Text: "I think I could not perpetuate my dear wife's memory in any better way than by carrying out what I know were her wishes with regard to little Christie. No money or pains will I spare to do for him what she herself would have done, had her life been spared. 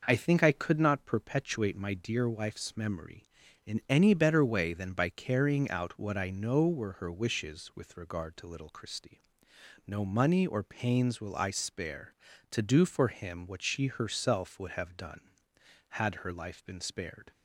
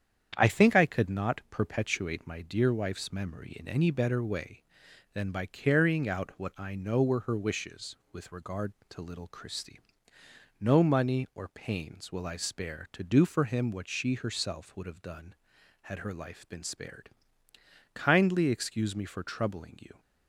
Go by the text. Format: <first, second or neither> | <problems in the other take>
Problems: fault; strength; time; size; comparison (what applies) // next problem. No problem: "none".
first | starts louder than the rest; strong; until 1.3 s; 8.5 dB // goes on to say "Kindly excuse me for troubling you"; strong; from 17.9 s on; 2.0 s long